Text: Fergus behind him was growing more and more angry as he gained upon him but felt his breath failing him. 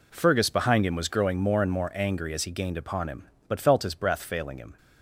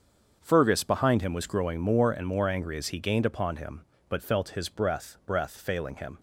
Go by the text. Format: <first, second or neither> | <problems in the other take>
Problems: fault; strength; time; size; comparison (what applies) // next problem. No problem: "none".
first | starts louder than the rest; until 1.4 s; 7 dB // says "breath" twice; at 5.2 s